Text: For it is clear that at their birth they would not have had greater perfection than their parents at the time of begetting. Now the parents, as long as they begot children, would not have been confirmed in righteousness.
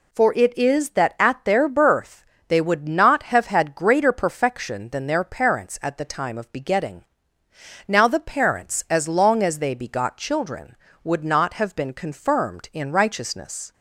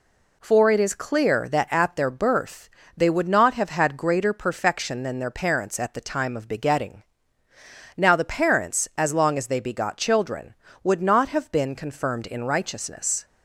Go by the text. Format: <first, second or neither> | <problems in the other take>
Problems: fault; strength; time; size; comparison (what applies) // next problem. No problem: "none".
second | skips "clear"; at 0.9 s // pauses between "birth" and "they"; slight; at 2.2 s; 0.24 s long; slight in the second